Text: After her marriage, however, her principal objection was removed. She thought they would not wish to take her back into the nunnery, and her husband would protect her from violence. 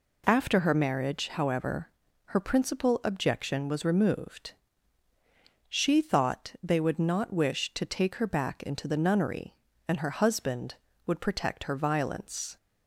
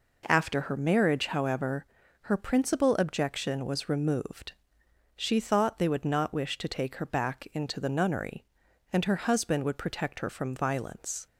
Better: second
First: skips "from"; at 11.7 s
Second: none

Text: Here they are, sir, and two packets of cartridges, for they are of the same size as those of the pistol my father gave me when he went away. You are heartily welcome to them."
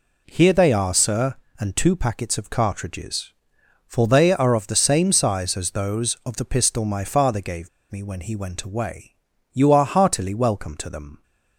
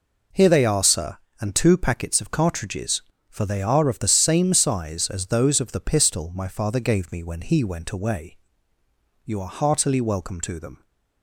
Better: second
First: pauses between "gave" and "me"; slight; at 7.6 s; 0.22 s long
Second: none

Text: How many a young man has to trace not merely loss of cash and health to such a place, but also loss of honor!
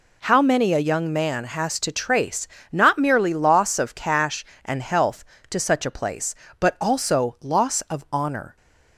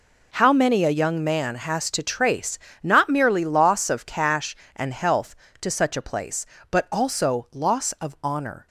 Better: first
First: pauses between "trace" and "not"; slight; at 2.4 s; 0.26 s long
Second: gets quieter; strong; throughout; 12 dB // pauses between "trace" and "not"; slight; at 2.5 s; 0.26 s long

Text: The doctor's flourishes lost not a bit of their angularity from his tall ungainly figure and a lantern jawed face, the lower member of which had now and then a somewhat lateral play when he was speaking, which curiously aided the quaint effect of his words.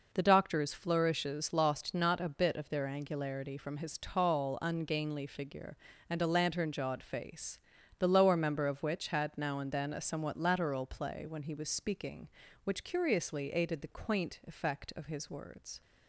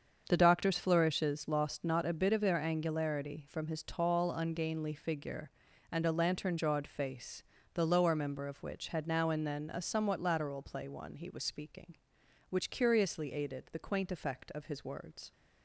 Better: first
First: none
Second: starts louder than the rest; until 1.2 s; 7 dB // says "one" for "when"; at 10.8 s

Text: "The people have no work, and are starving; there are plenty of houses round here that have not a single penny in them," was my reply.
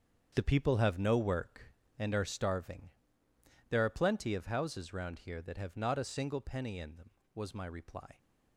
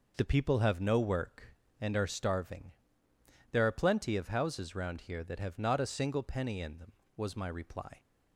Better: second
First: gets quieter; strong; throughout; 11 dB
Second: none

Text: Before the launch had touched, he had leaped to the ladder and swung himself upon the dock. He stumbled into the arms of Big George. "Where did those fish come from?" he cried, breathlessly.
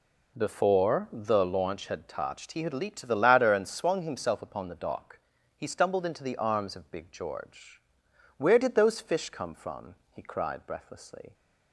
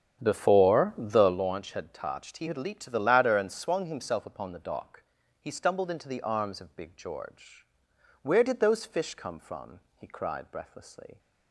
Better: first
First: none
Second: starts louder than the rest; strong; until 1.4 s; 8.5 dB

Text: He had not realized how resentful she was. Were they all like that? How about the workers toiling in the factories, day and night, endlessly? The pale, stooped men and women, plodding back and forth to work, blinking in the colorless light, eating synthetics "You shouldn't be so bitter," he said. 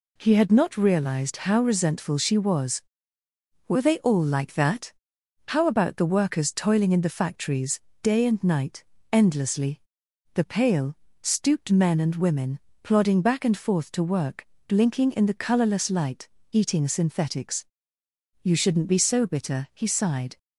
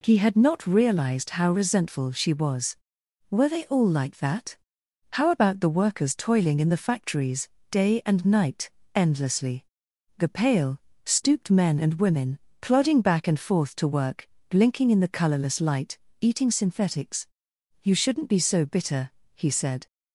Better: second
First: pauses between "synthetics" and "You"; noticeable; at 17.6 s; 0.76 s long // says "sighed" for "said"; at 19.8 s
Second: pauses between "synthetics" and "You"; noticeable; at 17.2 s; 0.56 s long

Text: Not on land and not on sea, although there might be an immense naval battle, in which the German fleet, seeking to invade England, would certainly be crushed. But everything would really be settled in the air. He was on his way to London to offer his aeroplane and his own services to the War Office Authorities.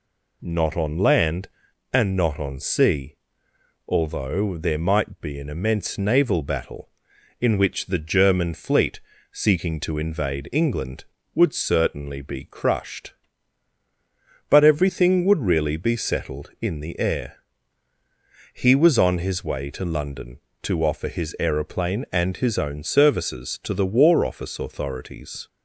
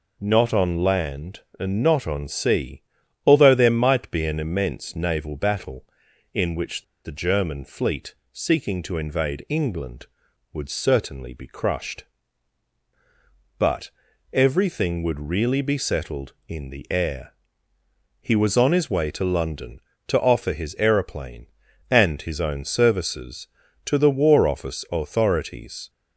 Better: first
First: none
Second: pauses between "which" and "the"; slight; at 6.8 s; 0.20 s long // pauses between "But" and "everything"; at 13.8 s; 0.42 s long

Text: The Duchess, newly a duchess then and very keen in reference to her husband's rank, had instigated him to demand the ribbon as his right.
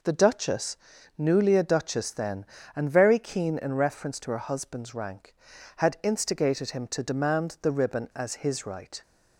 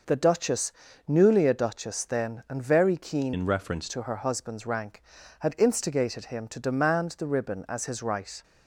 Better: first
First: none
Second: changes voice from "in" to "reference"; from 3.3 to 3.8 s; 0.5 s long

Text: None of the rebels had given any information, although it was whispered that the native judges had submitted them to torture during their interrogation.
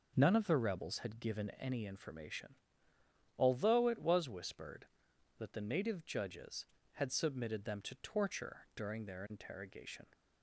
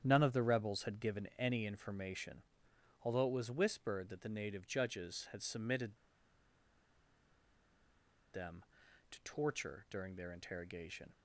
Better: first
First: none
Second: starts louder than the rest; strong; until 1.0 s; 9 dB // pauses between "submitted" and "them"; strong; at 5.9 s; 2.3 s long

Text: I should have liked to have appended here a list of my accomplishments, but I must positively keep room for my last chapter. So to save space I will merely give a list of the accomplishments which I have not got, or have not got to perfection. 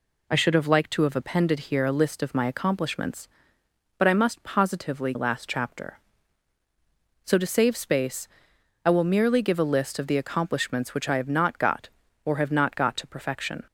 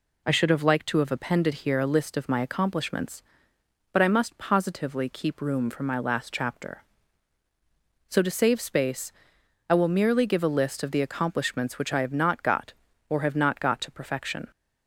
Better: second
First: skips "keep room for my"; at 5.1 s // pauses between "space" and "I"; noticeable; at 8.2 s; 0.60 s long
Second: pauses between "space" and "I"; noticeable; at 9.1 s; 0.60 s long

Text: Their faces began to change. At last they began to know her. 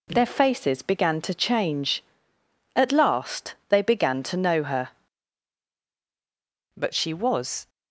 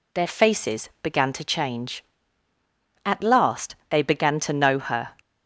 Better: second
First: goes on to say "But she was"; noticeable; from 6.7 s on; 0.94 s long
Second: none

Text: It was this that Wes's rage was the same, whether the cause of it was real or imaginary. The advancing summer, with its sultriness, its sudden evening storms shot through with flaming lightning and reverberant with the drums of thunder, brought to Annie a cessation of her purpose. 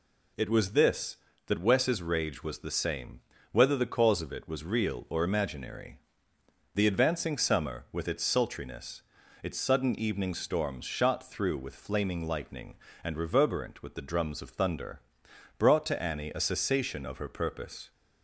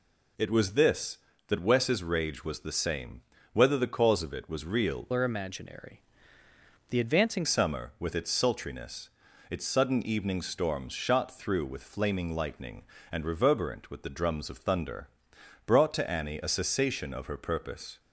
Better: first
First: none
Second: changes voice from "or" to "advancing"; from 5.1 to 7.4 s; 2.3 s long

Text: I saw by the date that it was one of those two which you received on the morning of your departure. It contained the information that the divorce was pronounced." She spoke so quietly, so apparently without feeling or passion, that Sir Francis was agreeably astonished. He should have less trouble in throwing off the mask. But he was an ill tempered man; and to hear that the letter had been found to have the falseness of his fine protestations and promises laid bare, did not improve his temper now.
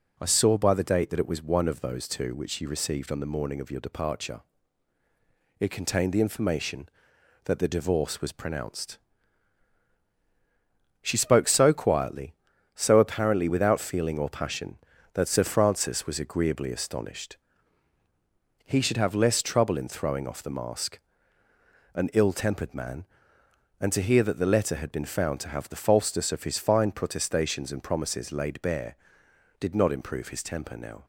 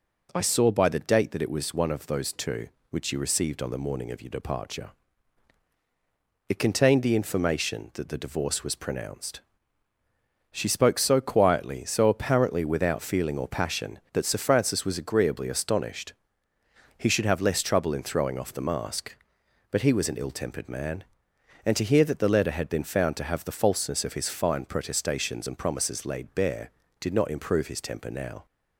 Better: second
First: skips "But he was"; at 21.4 s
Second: none

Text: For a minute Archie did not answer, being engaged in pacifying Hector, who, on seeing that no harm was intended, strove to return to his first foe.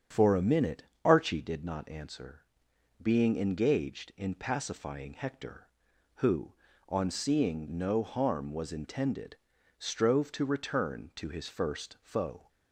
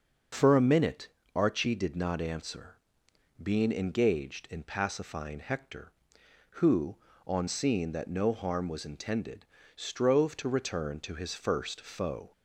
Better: second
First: starts louder than the rest; strong; until 1.3 s; 8 dB // pauses between "minute" and "Archie"; slight; at 0.8 s; 0.22 s long // skips "that"; at 7.6 s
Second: starts louder than the rest; until 1.6 s; 6 dB // pauses between "minute" and "Archie"; slight; at 1.0 s; 0.26 s long

